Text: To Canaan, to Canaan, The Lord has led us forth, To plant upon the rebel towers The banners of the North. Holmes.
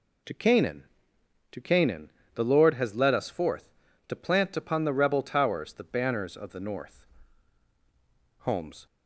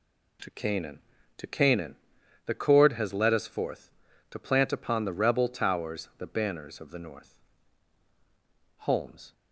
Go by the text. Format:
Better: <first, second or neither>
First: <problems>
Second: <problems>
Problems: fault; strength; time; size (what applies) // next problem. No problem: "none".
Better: first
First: none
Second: says "Cord" for "Lord"; at 2.5 s